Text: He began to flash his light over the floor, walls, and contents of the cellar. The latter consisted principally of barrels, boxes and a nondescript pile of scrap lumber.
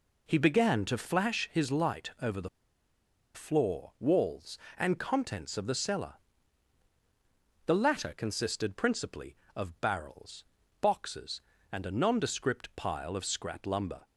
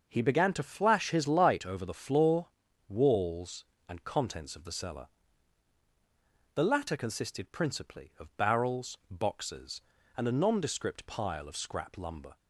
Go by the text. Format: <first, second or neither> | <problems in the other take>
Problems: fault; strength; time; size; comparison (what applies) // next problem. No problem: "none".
second | pauses between "the" and "floor"; noticeable; at 2.4 s; 0.86 s long